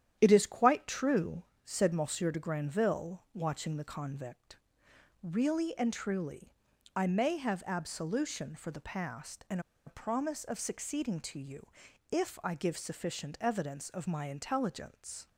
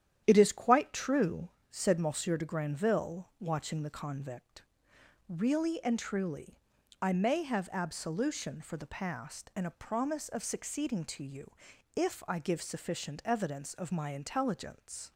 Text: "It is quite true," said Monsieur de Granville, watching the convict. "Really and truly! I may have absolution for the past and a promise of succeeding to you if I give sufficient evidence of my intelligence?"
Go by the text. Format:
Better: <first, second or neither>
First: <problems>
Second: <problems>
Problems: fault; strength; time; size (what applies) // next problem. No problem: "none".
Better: second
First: starts louder than the rest; strong; until 1.2 s; 10.5 dB // pauses between "and" and "a"; slight; at 9.5 s; 0.26 s long // pauses between "you" and "if"; at 11.6 s; 0.42 s long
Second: starts louder than the rest; strong; until 1.2 s; 10.5 dB // pauses between "you" and "if"; at 11.5 s; 0.42 s long